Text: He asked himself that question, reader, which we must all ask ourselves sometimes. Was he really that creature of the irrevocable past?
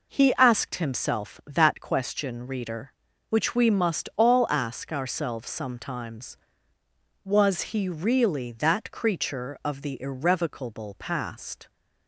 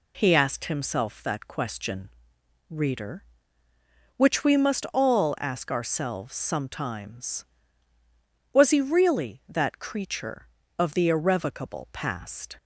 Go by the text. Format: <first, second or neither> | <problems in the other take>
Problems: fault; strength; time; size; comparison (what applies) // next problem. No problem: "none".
neither | none